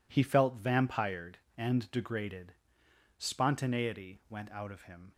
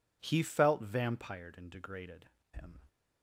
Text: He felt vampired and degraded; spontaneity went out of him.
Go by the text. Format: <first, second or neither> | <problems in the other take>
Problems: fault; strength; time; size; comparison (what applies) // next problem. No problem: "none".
first | skips "spontaneity went out of"; at 2.3 s